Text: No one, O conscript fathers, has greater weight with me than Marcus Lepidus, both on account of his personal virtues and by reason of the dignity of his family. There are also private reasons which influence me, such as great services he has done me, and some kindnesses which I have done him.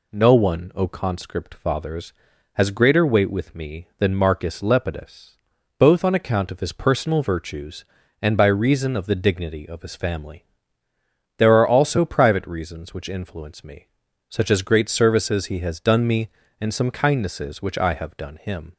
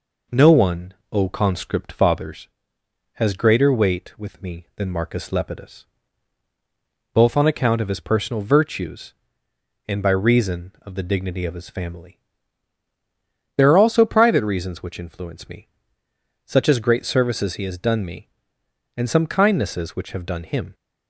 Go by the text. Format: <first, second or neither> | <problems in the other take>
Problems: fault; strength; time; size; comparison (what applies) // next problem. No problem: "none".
first | skips "I"; at 20.1 s